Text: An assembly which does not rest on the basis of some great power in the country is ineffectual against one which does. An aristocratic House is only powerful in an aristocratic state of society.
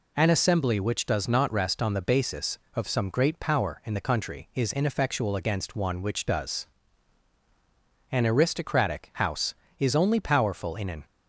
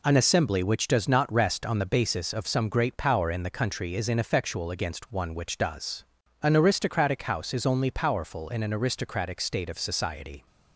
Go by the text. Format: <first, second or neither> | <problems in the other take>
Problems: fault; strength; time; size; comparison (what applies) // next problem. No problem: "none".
second | stops before "aristocratic state of society"; at 11.0 s